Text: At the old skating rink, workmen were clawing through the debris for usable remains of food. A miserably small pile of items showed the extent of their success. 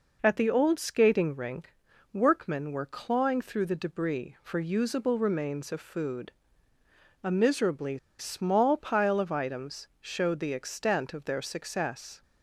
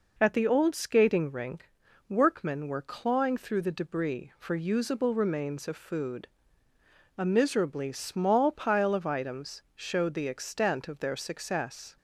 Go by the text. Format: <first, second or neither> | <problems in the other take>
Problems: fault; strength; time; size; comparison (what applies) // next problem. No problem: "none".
second | pauses between "miserably" and "small"; slight; at 7.9 s; 0.22 s long